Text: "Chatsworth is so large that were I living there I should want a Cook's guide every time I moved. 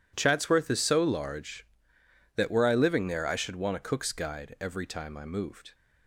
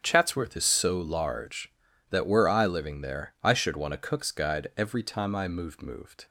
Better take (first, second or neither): first